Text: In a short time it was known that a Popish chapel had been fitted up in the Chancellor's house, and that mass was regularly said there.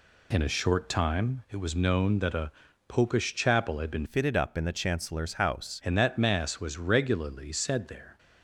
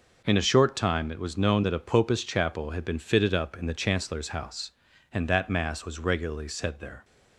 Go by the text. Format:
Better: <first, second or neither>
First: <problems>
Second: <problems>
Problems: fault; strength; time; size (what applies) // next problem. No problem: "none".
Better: second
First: pauses between "a" and "Popish"; slight; at 2.5 s; 0.36 s long // changes voice from "fitted" to "house"; from 4.0 to 5.8 s; 1.8 s long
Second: none